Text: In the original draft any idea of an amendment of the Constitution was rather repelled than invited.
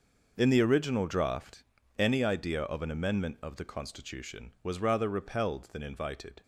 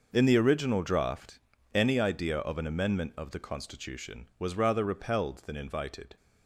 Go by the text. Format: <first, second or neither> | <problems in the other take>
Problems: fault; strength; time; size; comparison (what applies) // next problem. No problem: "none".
neither | pauses between "draft" and "any"; slight; the same in both